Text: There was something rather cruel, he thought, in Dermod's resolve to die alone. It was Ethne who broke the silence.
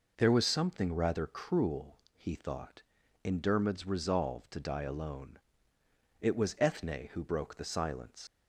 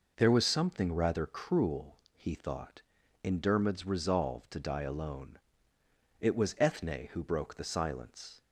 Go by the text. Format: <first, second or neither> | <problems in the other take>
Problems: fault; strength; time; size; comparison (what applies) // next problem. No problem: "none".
second | leaves "silence" unfinished; at 8.2 s; 140 ms